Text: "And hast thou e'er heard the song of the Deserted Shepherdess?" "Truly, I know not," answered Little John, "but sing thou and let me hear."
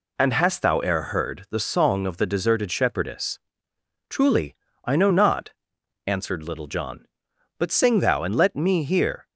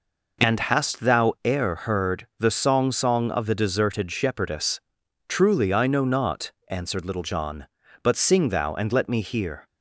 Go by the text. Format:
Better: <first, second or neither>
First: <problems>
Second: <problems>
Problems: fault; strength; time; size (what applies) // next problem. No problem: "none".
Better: first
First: none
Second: says "song" twice; at 2.9 s